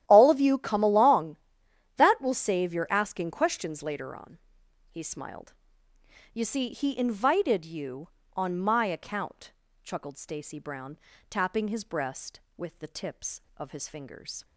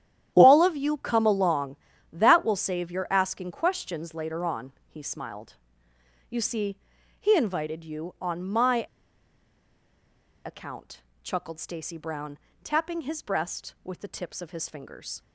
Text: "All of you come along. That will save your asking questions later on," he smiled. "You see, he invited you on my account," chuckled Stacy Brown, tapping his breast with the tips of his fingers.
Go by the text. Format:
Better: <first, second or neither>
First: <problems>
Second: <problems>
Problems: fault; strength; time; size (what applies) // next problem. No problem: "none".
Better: first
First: starts louder than the rest; strong; until 1.0 s; 11.5 dB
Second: starts louder than the rest; strong; until 1.3 s; 11 dB // pauses between "my" and "account"; strong; at 8.8 s; 1.6 s long